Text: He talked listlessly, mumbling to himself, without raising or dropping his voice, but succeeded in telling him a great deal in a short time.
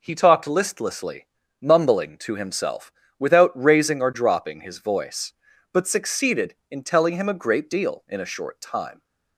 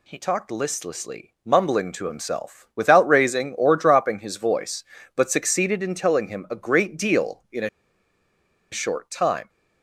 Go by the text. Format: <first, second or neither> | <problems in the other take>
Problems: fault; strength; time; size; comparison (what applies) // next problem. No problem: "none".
first | pauses between "a" and "short"; at 7.6 s; 1.0 s long